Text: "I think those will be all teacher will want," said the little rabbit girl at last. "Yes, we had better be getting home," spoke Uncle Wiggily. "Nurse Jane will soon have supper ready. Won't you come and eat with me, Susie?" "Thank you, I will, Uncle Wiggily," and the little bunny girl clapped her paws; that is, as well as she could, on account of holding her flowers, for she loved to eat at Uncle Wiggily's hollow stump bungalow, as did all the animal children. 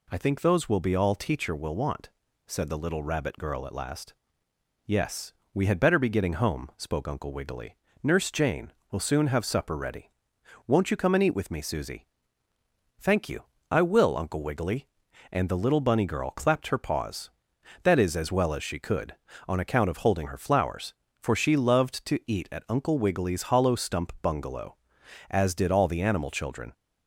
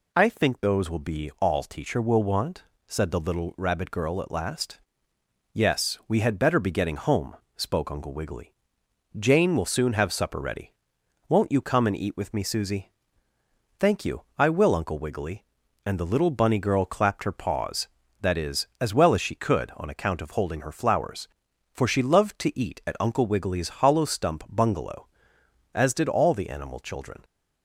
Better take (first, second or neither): first